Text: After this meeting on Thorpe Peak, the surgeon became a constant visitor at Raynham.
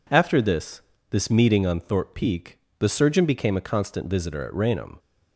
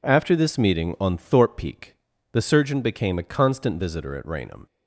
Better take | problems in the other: second | says "this" twice; at 1.0 s

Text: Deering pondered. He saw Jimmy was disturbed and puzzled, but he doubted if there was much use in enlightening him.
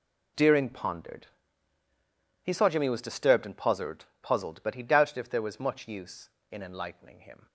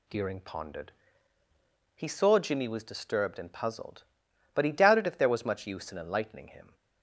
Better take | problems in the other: second | says "puzzled" twice; at 4.2 s

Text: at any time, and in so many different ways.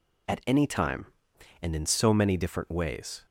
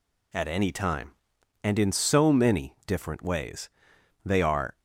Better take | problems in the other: first | goes on to say "They are"; from 4.2 s on; 0.56 s long

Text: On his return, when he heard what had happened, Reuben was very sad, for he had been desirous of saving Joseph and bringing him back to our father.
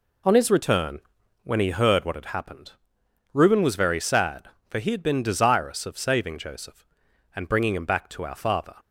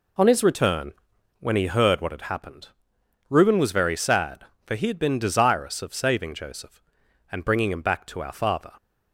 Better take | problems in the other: neither | none

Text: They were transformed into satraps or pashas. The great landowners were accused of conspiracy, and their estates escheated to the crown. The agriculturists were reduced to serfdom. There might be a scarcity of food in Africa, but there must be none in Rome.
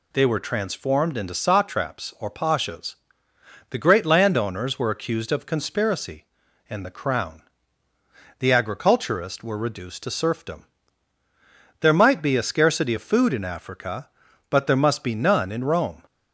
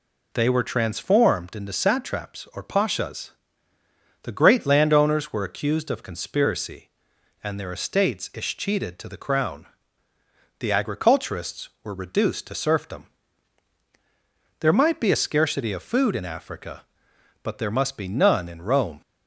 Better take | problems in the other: second | skips "their estates escheated to"; at 6.8 s

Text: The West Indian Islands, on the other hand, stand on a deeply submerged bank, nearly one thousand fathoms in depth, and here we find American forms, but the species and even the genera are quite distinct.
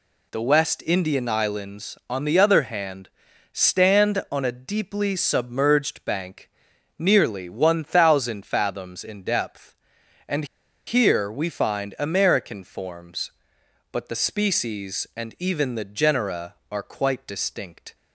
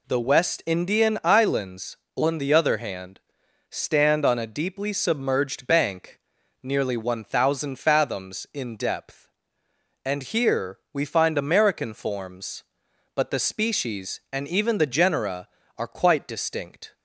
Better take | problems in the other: second | pauses between "and" and "here"; at 10.4 s; 0.41 s long

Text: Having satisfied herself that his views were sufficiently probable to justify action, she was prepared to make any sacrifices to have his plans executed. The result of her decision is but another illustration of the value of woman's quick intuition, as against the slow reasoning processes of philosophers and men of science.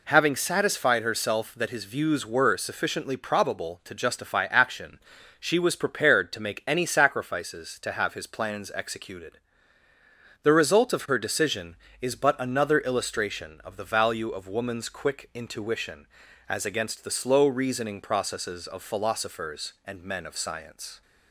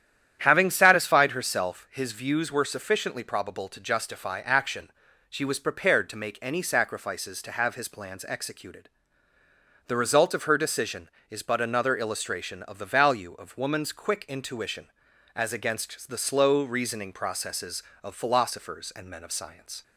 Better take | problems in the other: first | starts louder than the rest; strong; until 1.4 s; 10 dB // skips "that"; at 1.8 s

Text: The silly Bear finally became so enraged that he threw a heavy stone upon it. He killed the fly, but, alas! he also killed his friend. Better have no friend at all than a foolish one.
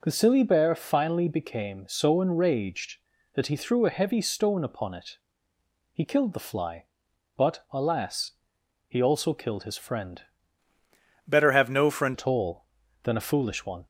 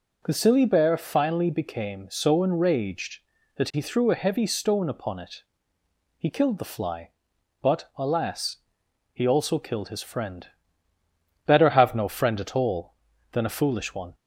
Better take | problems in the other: second | changes voice from "Better" to "friend"; from 11.2 to 12.1 s; 0.9 s long

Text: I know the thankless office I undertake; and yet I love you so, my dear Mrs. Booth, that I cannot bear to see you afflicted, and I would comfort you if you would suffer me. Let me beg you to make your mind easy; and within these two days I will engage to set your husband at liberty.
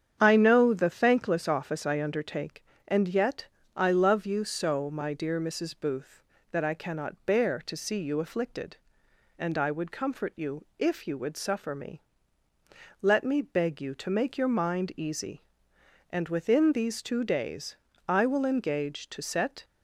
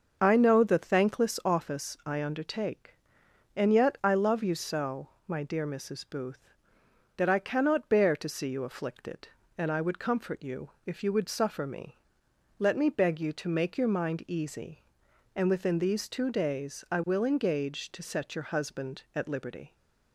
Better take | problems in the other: second | starts louder than the rest; strong; until 1.2 s; 8.5 dB; also in the second // pauses between "yet" and "I"; slight; at 3.4 s; 0.30 s long // pauses between "days" and "I"; slight; at 17.7 s; 0.30 s long // stops before "your husband at liberty"; at 19.6 s

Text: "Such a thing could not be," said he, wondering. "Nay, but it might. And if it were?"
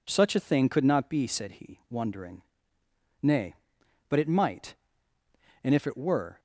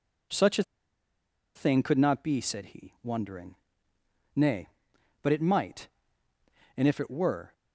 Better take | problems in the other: first | pauses between "a" and "thing"; noticeable; at 0.6 s; 0.93 s long

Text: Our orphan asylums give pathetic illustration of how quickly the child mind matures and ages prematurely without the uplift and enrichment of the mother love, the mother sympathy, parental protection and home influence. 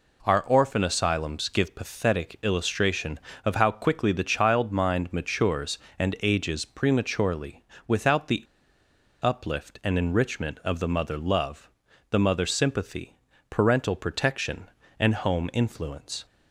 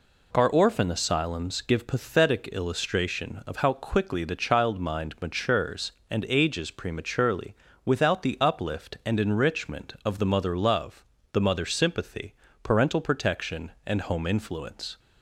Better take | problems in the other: second | pauses between "prematurely" and "without"; slight; at 7.6 s; 0.24 s long; slight in the second // pauses between "the" and "uplift"; noticeable; at 8.4 s; 0.78 s long

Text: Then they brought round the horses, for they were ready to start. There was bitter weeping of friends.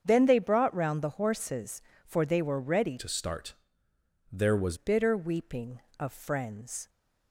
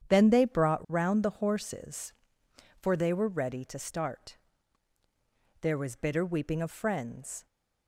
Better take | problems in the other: second | starts louder than the rest; strong; until 1.0 s; 7.5 dB; strong in the second // changes voice from "to" to "was"; from 2.9 to 4.7 s; 1.8 s long

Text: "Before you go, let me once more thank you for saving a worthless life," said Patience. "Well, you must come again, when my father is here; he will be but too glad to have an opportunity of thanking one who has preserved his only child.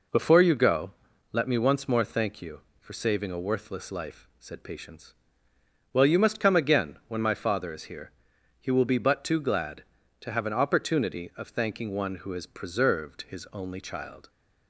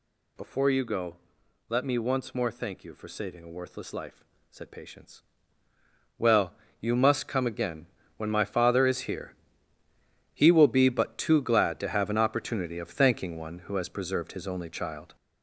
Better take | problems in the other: first | gets louder; noticeable; throughout; 4.5 dB

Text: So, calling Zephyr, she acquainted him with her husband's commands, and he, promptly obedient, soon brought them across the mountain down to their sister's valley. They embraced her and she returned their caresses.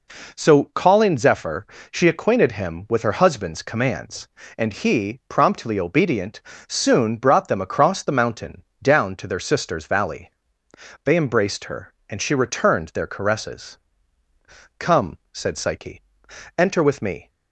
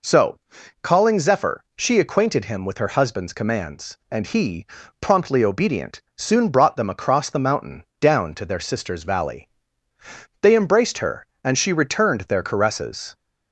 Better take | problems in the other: second | pauses between "mountain" and "down"; slight; at 8.6 s; 0.20 s long; slight in the second // goes on to say "Come said Psyche enter with me"; strong; from 14.7 s on; 2.5 s long

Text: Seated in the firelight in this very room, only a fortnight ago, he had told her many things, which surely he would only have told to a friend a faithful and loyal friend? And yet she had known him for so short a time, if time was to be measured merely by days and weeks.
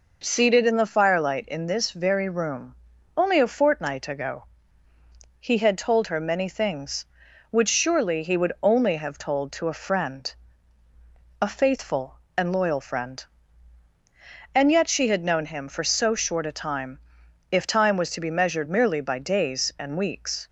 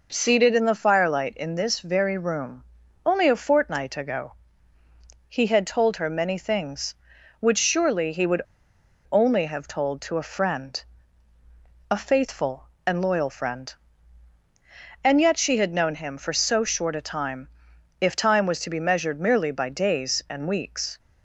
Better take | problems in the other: first | pauses between "would" and "only"; noticeable; at 8.4 s; 0.70 s long // pauses between "friend" and "a"; at 10.8 s; 1.1 s long; also in the first

